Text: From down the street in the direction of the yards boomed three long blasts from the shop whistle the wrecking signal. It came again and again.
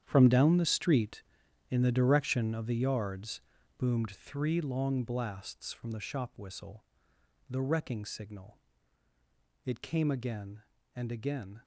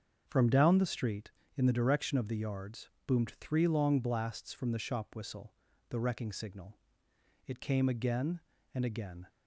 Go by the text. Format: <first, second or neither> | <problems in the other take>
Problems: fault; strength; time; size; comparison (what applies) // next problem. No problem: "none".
second | gets quieter; strong; throughout; 13.5 dB // starts louder than the rest; strong; until 1.0 s; 9.5 dB; also in the second // pauses between "yards" and "boomed"; slight; at 3.4 s; 0.36 s long; slight in the second // pauses between "whistle" and "the"; noticeable; at 6.8 s; 0.66 s long; slight in the second